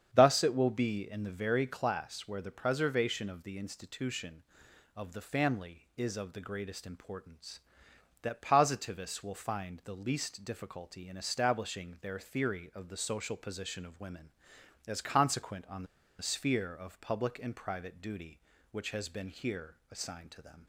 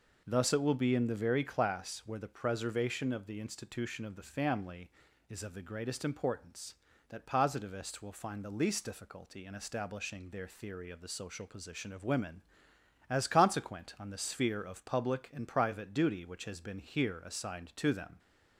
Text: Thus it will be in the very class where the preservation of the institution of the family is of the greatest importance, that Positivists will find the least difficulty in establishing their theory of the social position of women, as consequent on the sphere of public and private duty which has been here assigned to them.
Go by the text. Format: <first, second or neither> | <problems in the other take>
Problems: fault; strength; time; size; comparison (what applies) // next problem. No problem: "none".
second | starts louder than the rest; strong; until 1.1 s; 8 dB // pauses between "on" and "the"; slight; at 15.8 s; 0.35 s long